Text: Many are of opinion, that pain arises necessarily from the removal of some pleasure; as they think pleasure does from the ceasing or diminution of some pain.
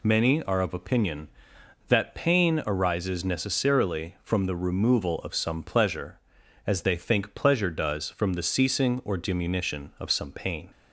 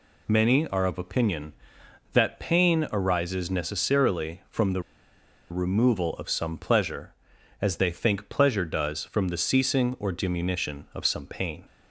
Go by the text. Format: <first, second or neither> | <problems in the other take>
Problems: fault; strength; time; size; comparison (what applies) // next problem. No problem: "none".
first | pauses between "the" and "removal"; noticeable; at 4.8 s; 0.69 s long